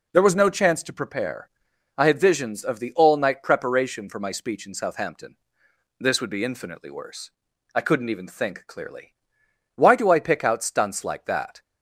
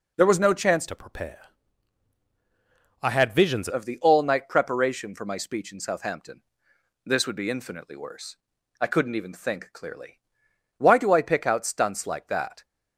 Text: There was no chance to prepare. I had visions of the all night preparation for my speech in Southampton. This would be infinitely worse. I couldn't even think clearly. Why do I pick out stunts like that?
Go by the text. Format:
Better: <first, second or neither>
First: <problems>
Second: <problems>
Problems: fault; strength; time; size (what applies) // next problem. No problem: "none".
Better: first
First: none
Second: changes voice from "to" to "visions"; from 0.8 to 3.6 s; 2.8 s long